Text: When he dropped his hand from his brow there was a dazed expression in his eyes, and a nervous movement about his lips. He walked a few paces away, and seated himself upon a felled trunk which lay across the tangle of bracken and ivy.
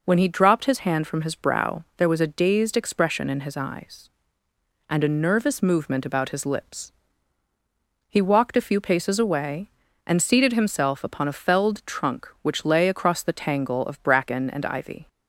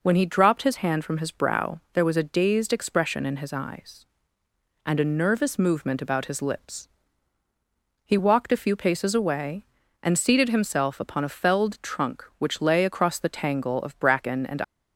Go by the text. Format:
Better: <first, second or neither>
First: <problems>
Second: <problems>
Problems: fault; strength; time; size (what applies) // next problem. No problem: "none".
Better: first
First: none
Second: stops before "ivy"; at 14.6 s